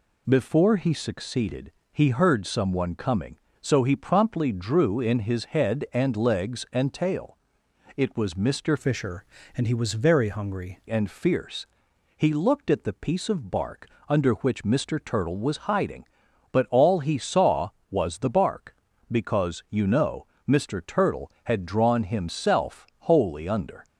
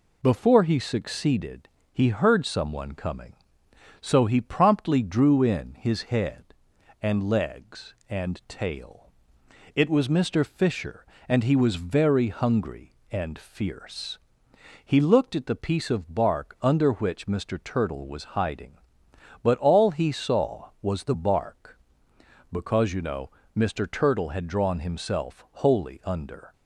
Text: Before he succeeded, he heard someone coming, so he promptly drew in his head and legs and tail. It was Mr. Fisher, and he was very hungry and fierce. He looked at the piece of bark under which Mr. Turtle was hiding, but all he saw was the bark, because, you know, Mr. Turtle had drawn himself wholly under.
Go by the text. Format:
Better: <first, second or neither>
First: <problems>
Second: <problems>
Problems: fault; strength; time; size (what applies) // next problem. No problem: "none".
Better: second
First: changes voice from "Fisher" to "hungry"; from 8.7 to 10.7 s; 2.0 s long // pauses between "bark" and "under"; slight; at 13.8 s; 0.18 s long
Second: none